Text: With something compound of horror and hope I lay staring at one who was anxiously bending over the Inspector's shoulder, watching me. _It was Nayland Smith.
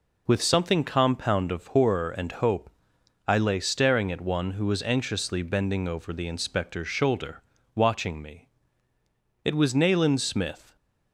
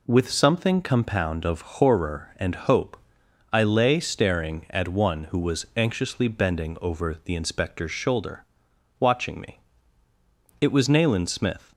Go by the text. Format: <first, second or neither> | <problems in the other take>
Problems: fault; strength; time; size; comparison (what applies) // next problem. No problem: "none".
neither | pauses between "hope" and "I"; noticeable; the same in both